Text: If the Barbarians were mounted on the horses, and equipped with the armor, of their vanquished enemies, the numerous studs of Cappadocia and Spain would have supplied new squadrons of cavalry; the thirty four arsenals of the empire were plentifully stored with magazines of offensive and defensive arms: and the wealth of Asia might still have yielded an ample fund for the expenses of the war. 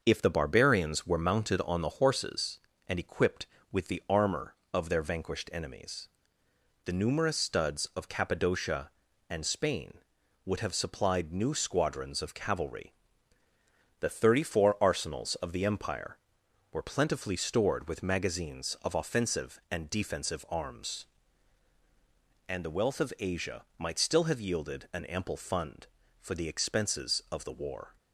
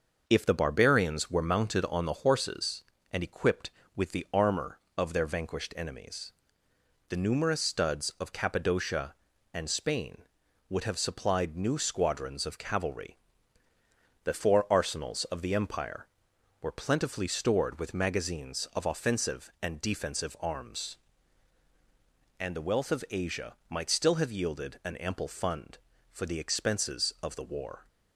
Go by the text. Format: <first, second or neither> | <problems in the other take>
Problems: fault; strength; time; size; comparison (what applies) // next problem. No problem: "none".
first | starts louder than the rest; until 1.2 s; 6 dB; also in the first // skips "thirty"; at 14.3 s